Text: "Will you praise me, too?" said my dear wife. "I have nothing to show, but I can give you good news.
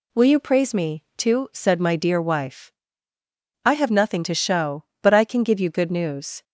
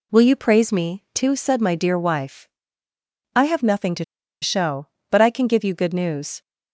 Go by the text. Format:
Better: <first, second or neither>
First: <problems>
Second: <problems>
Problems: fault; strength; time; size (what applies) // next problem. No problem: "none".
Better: first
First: none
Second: pauses between "to" and "show"; at 4.0 s; 0.38 s long